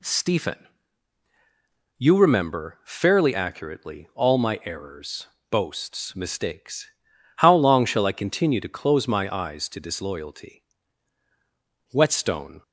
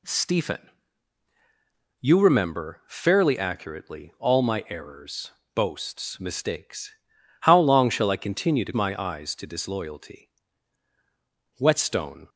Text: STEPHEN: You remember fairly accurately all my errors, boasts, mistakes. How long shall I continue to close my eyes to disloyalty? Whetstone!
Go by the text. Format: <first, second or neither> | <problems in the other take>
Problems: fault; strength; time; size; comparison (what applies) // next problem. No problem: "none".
first | skips "close"; at 8.7 s